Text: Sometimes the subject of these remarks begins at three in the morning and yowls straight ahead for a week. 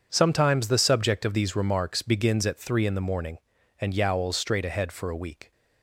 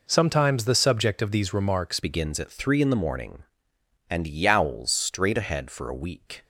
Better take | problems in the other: first | changes voice at "begins"; from 1.9 s on; 4.5 s long

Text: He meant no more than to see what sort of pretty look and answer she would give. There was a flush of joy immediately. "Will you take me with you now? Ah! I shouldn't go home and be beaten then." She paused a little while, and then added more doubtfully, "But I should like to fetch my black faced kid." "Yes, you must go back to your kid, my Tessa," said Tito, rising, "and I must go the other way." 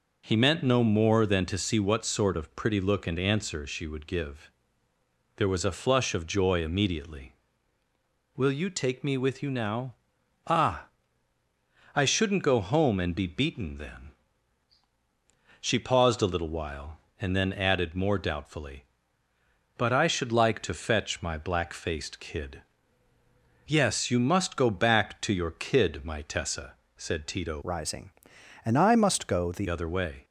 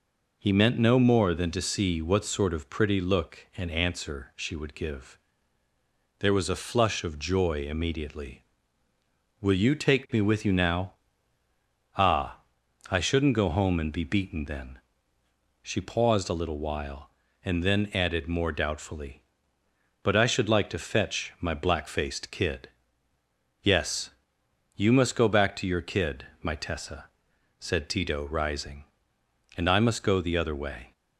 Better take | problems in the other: second | changes voice from "rising" to "the"; from 27.6 to 29.6 s; 2.0 s long

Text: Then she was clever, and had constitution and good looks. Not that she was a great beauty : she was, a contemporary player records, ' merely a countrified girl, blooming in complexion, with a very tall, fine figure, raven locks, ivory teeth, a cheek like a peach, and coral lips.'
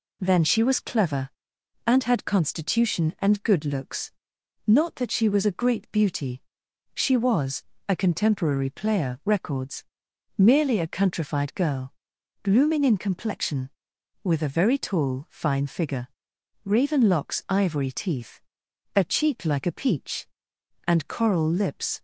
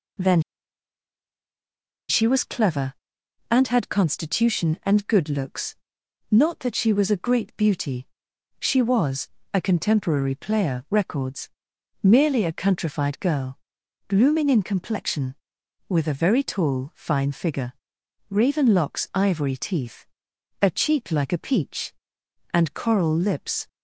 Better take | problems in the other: first | pauses between "Then" and "she"; strong; at 0.4 s; 1.6 s long

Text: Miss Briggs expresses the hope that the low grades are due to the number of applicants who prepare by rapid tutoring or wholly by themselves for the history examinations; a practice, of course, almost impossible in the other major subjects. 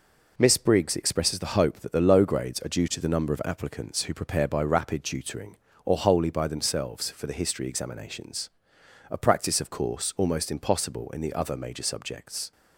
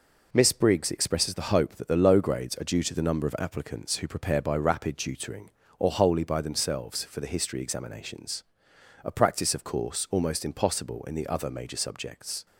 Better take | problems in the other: neither | none

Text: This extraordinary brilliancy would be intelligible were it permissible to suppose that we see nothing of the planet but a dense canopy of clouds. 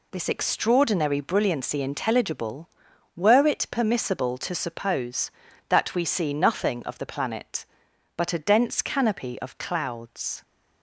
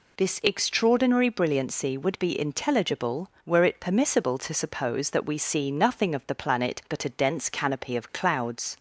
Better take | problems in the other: second | skips "would be"; at 1.8 s

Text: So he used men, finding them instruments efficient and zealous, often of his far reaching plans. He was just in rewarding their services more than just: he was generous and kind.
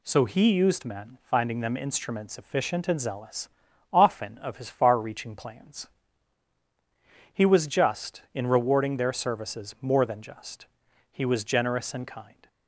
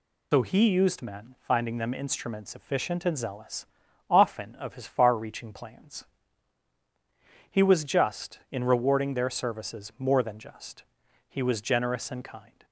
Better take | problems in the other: first | loses the start of "So"; at 0.3 s; 105 ms

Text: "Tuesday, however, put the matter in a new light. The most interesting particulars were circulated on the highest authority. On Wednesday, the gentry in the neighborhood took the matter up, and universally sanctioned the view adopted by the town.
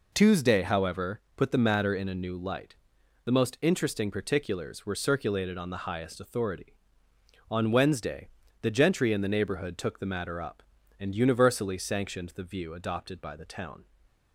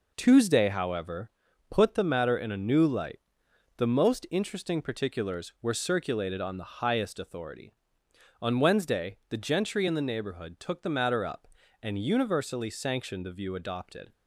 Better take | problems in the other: first | stops before "by the town"; at 14.1 s

